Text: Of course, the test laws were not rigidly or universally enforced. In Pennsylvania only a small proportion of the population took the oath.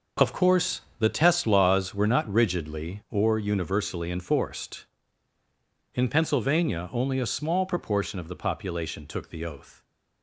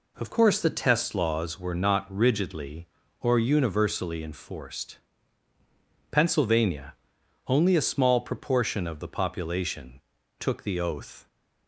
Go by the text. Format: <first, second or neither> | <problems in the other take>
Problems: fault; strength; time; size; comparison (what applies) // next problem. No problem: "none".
first | skips "In"; at 5.5 s // pauses between "Pennsylvania" and "only"; noticeable; at 6.9 s; 0.54 s long // pauses between "population" and "took"; at 10.0 s; 0.38 s long